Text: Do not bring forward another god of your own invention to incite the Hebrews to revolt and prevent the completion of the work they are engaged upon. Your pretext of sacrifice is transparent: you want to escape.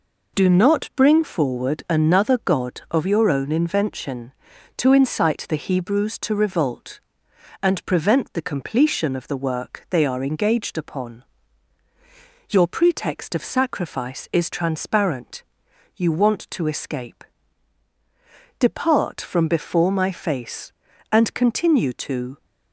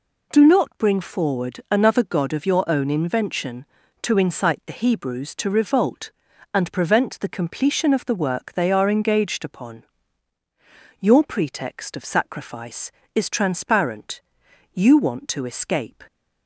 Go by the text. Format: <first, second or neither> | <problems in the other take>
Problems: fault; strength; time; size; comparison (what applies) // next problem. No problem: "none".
second | goes on to say "Depart from before my face and continue to"; strong; from 18.5 s on; 3.8 s long